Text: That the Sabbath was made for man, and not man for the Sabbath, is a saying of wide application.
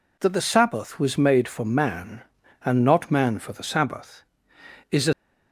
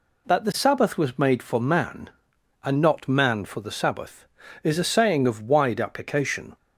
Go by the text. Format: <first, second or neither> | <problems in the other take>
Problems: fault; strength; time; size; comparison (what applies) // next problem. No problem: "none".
second | stops before "saying of wide application"; at 5.1 s